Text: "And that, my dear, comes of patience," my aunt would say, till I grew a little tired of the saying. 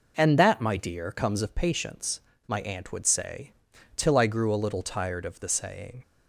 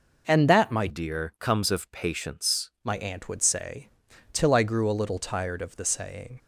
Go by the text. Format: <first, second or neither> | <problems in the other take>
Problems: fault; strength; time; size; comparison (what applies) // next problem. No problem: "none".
first | changes voice from "dear" to "patience"; from 0.8 to 2.7 s; 1.9 s long